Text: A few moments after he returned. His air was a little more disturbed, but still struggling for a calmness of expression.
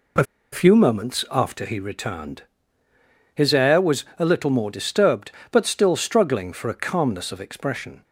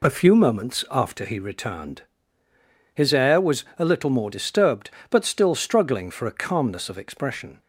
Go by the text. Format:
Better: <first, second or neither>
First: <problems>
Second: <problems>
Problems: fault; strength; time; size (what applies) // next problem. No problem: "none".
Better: second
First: pauses between "A" and "few"; slight; at 0.2 s; 0.29 s long // pauses between "was" and "a"; slight; at 4.0 s; 0.16 s long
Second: pauses between "was" and "a"; slight; at 3.6 s; 0.16 s long